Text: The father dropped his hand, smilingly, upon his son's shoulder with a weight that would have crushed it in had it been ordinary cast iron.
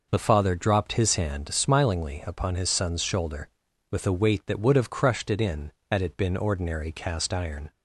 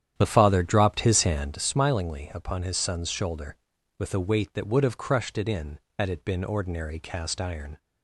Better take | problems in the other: first | starts louder than the rest; strong; until 1.6 s; 10 dB

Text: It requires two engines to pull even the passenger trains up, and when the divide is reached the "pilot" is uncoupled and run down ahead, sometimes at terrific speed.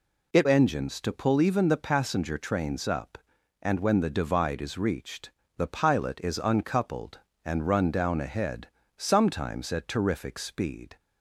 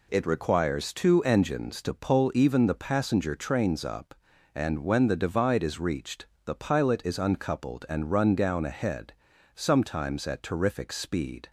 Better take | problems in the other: second | skips "requires two"; at 0.4 s // pauses between "reached" and "the"; slight; at 5.2 s; 0.26 s long; slight in the second

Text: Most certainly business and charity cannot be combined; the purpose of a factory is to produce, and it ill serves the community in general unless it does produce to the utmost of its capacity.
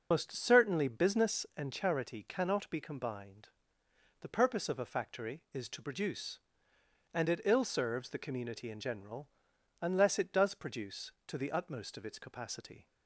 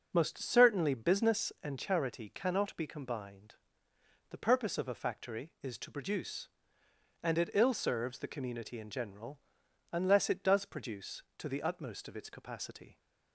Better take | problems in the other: second | loses the start of "Most"; at 0.1 s; 25 ms // starts louder than the rest; noticeable; until 1.1 s; 6 dB; also in the second // pauses between "general" and "unless"; noticeable; at 9.2 s; 0.52 s long; noticeable in the second

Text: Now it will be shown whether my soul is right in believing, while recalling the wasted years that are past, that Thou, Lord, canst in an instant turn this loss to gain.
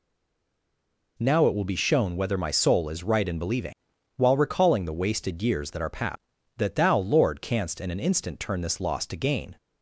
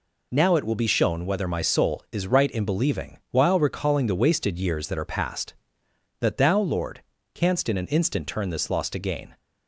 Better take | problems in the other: second | stays silent before the first word; noticeable; until 1.1 s; 1.1 s long

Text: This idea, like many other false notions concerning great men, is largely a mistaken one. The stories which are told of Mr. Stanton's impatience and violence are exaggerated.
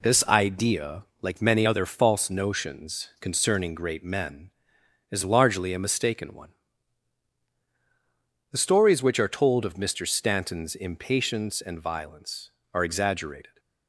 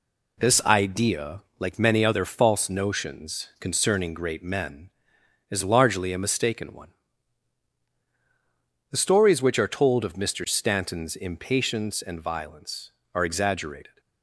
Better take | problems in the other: neither | none

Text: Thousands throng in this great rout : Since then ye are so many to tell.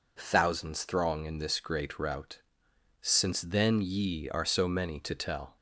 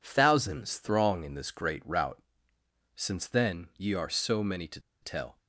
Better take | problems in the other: first | pauses between "to" and "tell"; slight; at 4.8 s; 0.21 s long

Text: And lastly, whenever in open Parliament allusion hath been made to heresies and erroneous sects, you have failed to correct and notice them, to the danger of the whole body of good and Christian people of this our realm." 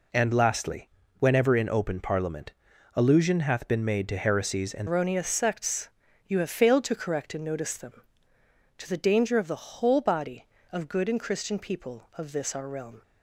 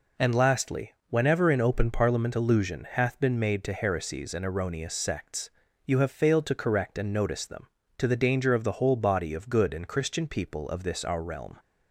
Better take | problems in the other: second | pauses between "Parliament" and "allusion"; at 2.5 s; 0.42 s long // changes voice at "erroneous"; from 4.8 s on; 8.2 s long

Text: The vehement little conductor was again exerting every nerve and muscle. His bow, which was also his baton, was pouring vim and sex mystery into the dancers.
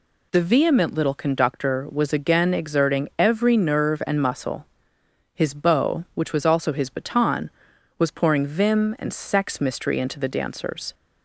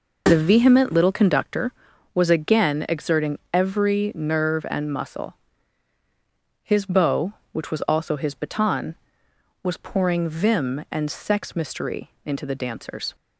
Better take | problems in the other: neither | none

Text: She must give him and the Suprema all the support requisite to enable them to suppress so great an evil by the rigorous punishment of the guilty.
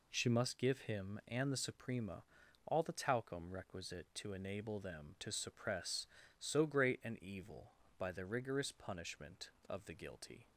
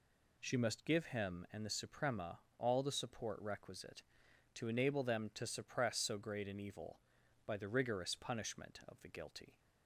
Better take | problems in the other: second | pauses between "Suprema" and "all"; at 2.2 s; 0.44 s long; slight in the second // says "talcum" for "support"; at 2.9 s

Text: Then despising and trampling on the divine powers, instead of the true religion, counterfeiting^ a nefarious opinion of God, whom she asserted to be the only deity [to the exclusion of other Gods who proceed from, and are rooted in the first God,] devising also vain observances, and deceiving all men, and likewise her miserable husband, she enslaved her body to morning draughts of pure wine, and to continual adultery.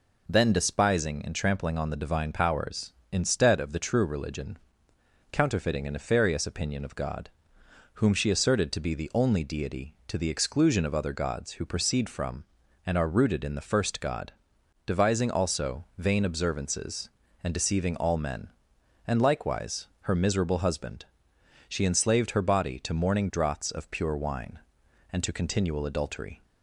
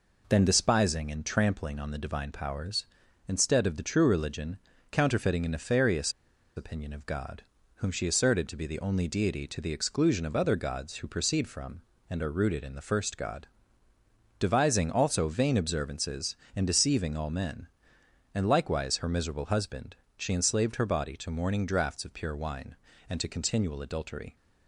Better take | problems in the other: first | pauses between "nefarious" and "opinion"; at 6.1 s; 0.44 s long

